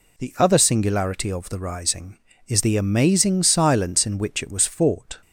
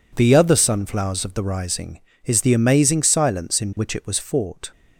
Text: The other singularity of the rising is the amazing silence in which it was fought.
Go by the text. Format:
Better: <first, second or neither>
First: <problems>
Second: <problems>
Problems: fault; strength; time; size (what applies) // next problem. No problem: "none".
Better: first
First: none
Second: says "sunflowers" for "singularity"; at 0.5 s